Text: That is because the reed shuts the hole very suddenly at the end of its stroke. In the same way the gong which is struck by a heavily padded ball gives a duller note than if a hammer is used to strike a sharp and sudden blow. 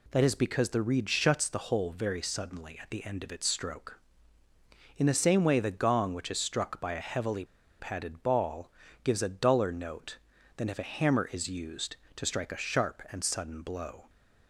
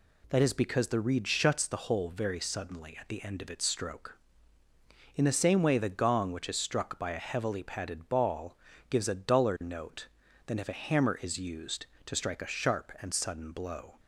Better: second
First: pauses between "heavily" and "padded"; slight; at 7.4 s; 0.34 s long // pauses between "ball" and "gives"; slight; at 8.7 s; 0.32 s long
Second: pauses between "ball" and "gives"; slight; at 8.5 s; 0.32 s long

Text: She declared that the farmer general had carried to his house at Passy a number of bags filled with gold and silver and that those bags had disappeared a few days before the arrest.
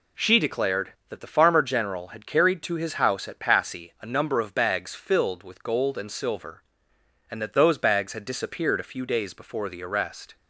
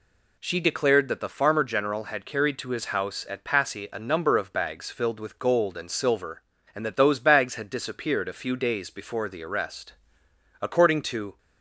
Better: first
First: none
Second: goes on to say "According to"; noticeable; from 10.6 s on; 0.76 s long

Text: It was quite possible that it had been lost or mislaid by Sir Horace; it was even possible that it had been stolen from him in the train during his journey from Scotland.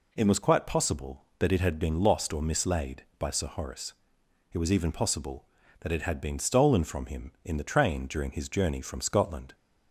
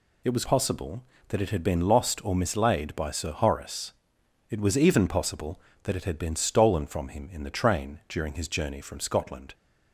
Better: first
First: none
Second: skips "quite"; at 0.4 s

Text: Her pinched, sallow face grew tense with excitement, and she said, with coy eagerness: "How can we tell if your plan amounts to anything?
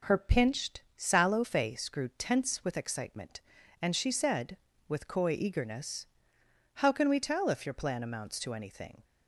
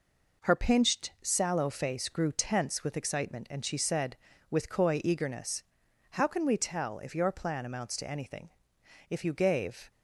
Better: first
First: none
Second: goes on to say "If you gave"; noticeable; from 9.0 s on; 0.82 s long

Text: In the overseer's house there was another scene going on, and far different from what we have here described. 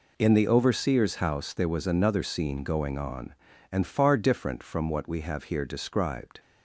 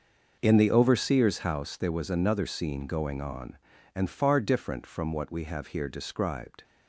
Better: first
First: none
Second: starts louder than the rest; noticeable; until 1.4 s; 6 dB

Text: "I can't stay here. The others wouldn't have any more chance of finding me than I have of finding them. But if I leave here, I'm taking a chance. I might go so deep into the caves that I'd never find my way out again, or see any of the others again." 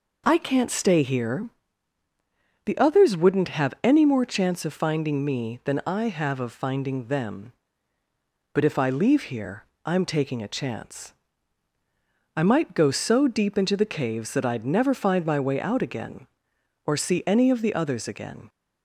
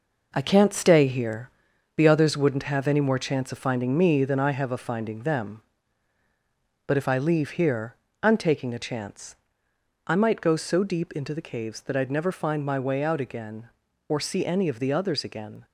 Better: first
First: none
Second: gets quieter; throughout; 6.5 dB

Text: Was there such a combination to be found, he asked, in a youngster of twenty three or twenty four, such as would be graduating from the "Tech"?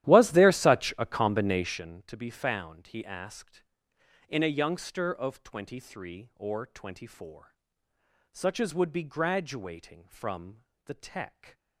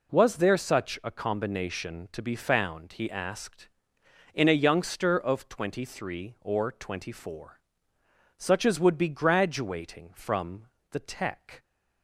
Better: second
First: starts louder than the rest; strong; until 1.9 s; 13 dB // pauses between "from" and "the"; slight; at 10.6 s; 0.24 s long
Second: pauses between "from" and "the"; slight; at 10.6 s; 0.24 s long

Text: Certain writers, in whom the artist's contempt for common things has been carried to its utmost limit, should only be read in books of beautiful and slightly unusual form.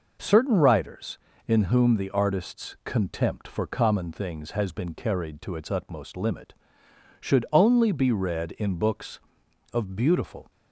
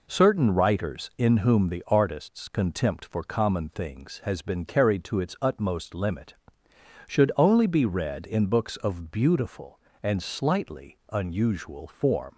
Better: second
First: stops before "and slightly unusual form"; at 10.4 s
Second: none

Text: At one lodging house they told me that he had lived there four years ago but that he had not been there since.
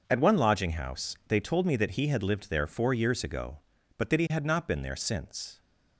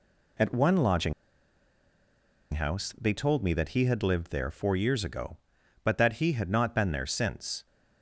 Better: first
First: none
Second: pauses between "lodging" and "house"; strong; at 1.1 s; 1.4 s long

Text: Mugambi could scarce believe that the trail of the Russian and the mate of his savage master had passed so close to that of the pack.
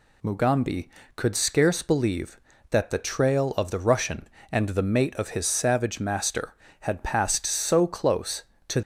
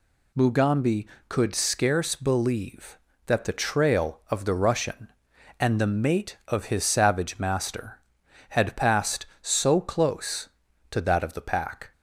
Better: second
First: stops before "that of the pack"; at 8.8 s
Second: none

